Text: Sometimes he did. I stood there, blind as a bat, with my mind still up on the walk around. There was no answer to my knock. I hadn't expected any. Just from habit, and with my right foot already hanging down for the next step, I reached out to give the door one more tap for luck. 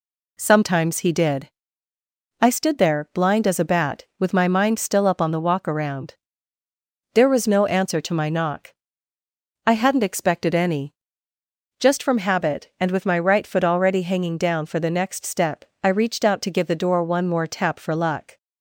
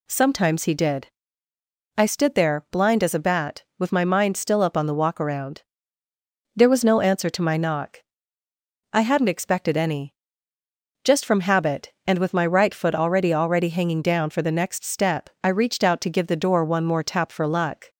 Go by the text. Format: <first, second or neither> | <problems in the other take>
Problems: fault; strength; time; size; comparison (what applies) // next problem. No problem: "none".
first | says "already" twice; at 13.3 s